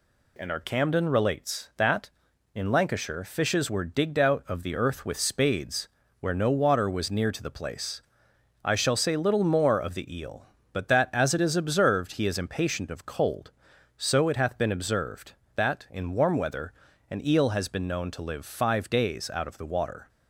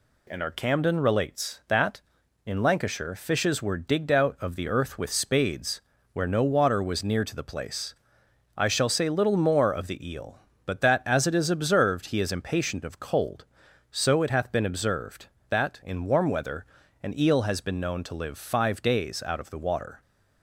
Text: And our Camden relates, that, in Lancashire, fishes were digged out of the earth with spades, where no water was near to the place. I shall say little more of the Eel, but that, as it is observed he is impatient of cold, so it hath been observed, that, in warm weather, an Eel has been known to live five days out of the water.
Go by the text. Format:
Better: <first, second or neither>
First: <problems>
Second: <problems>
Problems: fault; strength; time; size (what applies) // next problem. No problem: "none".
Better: neither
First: none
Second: none